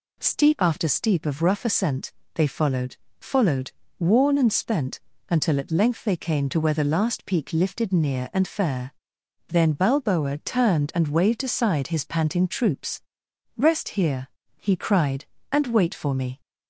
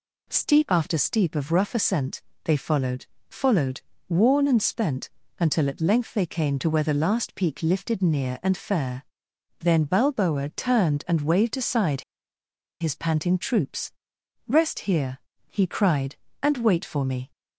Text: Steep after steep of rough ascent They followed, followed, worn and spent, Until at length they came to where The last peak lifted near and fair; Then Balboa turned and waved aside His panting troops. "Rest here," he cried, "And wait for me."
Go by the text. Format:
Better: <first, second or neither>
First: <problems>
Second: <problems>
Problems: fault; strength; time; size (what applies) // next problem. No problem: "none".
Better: first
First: pauses between "ascent" and "They"; slight; at 2.1 s; 0.22 s long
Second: pauses between "ascent" and "They"; slight; at 2.2 s; 0.22 s long // pauses between "aside" and "His"; noticeable; at 12.0 s; 0.78 s long